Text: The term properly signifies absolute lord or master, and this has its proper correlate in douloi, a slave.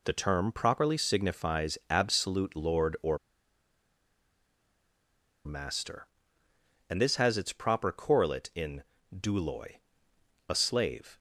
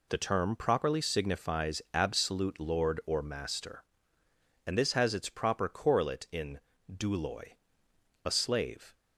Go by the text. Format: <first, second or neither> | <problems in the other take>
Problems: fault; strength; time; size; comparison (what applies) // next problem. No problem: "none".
second | pauses between "or" and "master"; strong; at 3.1 s; 2.2 s long // pauses between "in" and "douloi"; slight; at 8.8 s; 0.28 s long; slight in the second